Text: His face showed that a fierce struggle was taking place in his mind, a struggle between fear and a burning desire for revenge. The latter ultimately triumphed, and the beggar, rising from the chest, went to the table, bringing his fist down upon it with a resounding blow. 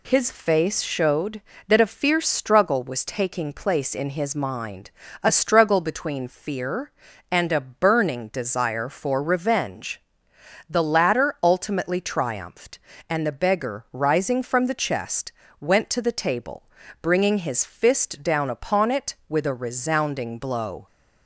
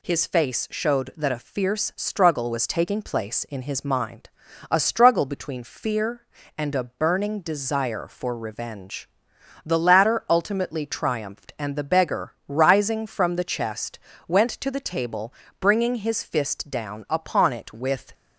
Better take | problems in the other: first | stops before "a resounding blow"; at 18.1 s

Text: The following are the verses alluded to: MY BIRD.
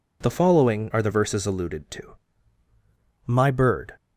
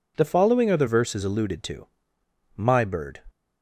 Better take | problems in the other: neither | none

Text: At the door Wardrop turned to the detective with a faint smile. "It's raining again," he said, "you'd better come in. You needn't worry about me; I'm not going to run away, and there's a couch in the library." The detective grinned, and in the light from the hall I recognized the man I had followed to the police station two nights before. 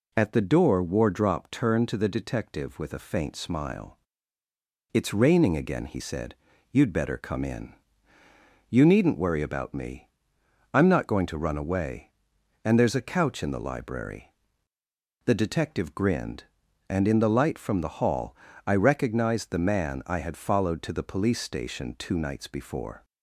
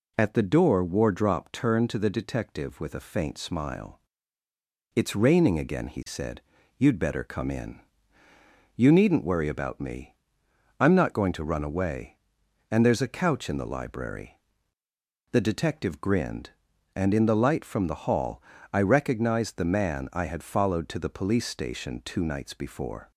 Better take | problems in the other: neither | pauses between "hall" and "I"; slight; the same in both

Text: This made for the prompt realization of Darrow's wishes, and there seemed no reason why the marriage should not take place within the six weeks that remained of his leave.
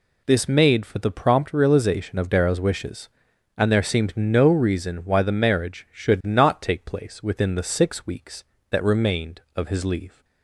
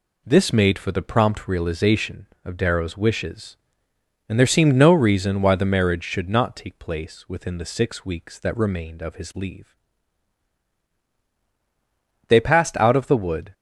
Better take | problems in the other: first | goes on to say "They passed out of the wood"; noticeable; from 12.2 s on; 1.2 s long

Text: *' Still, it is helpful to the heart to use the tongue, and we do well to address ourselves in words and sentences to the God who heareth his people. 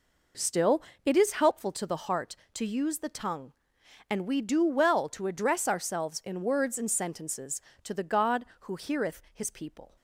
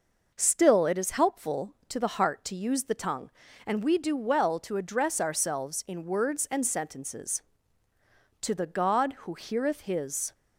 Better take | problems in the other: first | stops before "people"; at 10.3 s

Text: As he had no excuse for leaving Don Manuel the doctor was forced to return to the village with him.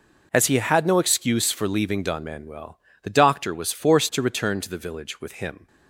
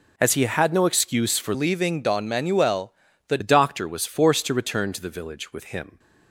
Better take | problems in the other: first | changes voice from "leaving" to "the"; from 1.5 to 3.3 s; 1.8 s long // pauses between "Manuel" and "the"; slight; at 2.9 s; 0.34 s long; slight in the first

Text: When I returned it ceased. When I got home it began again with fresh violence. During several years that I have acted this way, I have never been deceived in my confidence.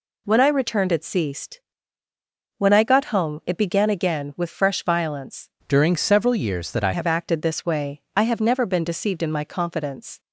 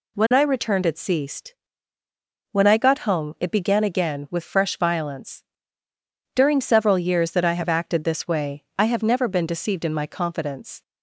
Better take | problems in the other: second | changes voice from "During" to "I"; from 5.6 to 6.9 s; 1.3 s long

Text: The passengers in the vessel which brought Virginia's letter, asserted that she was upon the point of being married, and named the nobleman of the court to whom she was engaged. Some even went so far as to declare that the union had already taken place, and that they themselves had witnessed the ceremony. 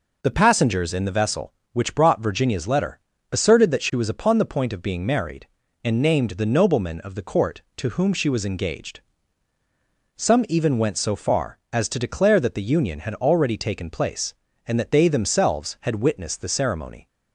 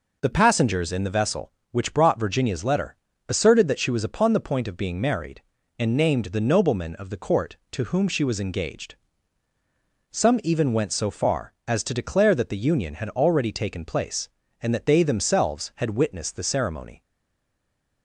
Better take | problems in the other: first | stays silent after the last word; from 17.0 s on; 1.0 s long

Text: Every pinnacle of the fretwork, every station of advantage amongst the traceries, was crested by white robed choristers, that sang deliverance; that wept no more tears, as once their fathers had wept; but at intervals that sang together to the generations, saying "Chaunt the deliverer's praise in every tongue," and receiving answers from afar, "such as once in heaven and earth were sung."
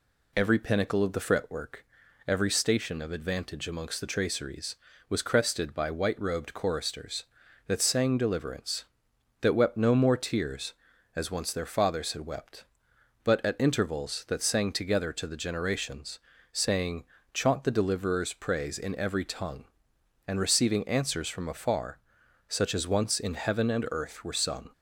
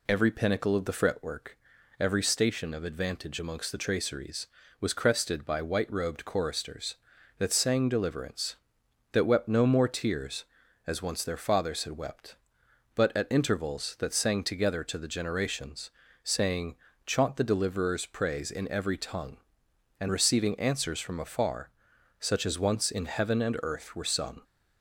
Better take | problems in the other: neither | pauses between "saying" and "Chaunt"; slight; the same in both

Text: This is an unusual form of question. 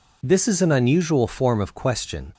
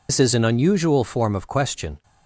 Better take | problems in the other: first | loses the start of "This"; at 0.0 s; 85 ms

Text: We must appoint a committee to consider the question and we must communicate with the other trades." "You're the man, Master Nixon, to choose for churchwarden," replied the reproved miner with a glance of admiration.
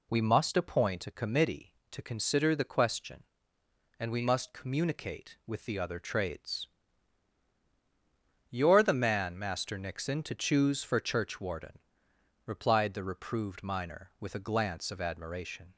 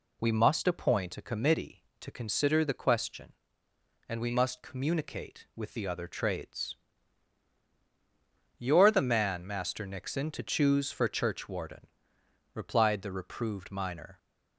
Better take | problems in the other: first | stops before "with a glance of admiration"; at 14.1 s

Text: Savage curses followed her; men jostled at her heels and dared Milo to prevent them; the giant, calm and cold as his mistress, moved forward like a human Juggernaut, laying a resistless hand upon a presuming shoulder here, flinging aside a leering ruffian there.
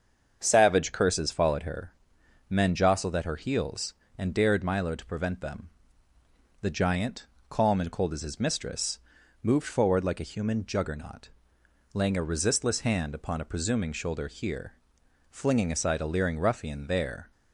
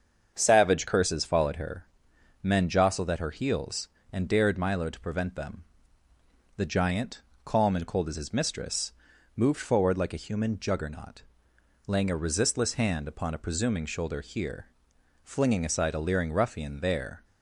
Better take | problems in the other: neither | starts louder than the rest; the same in both

